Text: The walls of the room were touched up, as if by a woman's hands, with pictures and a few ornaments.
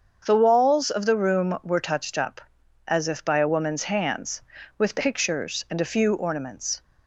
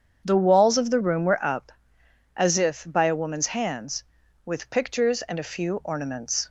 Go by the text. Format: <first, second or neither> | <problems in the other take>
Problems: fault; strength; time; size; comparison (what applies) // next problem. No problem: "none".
first | starts louder than the rest; strong; until 1.2 s; 7.5 dB; also in the first // skips "touched"; at 1.4 s